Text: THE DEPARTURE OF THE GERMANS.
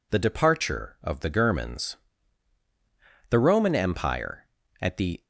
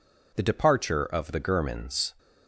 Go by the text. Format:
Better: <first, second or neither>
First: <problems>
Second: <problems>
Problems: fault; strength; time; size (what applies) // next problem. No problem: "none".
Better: second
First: goes on to say "The Roman Empire at the"; strong; from 3.3 s on; 1.9 s long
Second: none